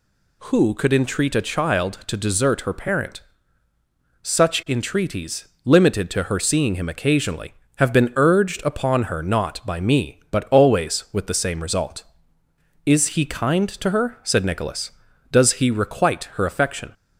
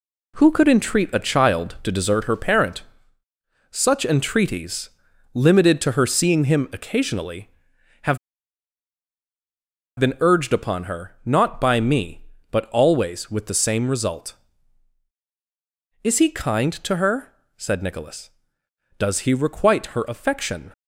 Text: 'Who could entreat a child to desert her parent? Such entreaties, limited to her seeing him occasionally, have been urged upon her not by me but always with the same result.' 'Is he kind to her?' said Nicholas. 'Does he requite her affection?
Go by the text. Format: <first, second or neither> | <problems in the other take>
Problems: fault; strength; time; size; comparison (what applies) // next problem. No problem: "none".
first | pauses between "have" and "been"; strong; at 8.1 s; 1.8 s long